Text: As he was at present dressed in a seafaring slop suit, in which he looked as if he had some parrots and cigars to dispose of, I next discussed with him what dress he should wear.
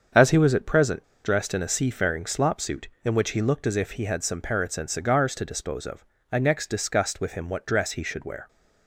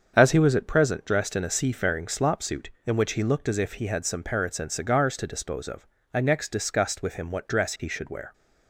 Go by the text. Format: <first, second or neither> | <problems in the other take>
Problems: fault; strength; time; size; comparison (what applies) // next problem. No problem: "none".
second | starts louder than the rest; until 1.3 s; 7 dB; also in the second // pauses between "present" and "dressed"; slight; at 1.0 s; 0.21 s long